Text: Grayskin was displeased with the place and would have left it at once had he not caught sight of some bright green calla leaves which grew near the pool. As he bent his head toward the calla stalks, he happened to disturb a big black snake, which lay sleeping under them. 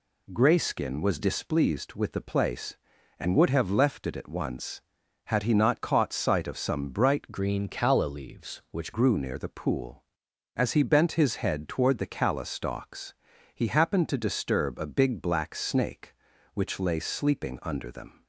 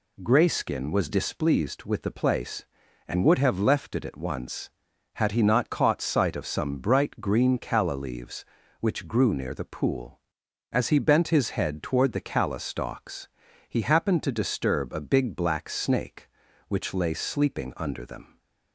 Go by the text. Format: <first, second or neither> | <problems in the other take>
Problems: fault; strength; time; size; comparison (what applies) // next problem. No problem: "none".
second | changes voice from "green" to "which"; from 7.3 to 8.9 s; 1.6 s long